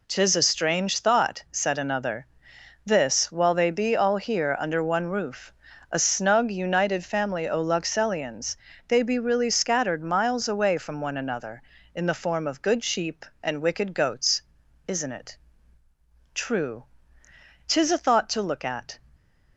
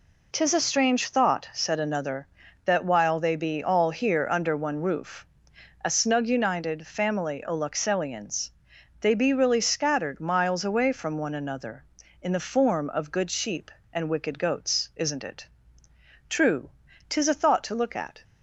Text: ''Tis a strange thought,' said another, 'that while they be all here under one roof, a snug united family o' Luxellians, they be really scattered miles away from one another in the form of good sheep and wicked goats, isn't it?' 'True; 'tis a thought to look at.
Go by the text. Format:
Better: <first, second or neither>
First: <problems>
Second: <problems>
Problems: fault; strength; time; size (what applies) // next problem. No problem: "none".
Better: second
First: says "this" for "that"; at 2.8 s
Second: none